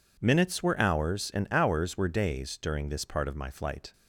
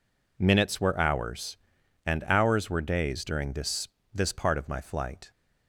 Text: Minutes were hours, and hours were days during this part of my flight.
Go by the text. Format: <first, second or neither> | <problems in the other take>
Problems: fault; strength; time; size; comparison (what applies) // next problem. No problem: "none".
first | says "this" twice; at 4.1 s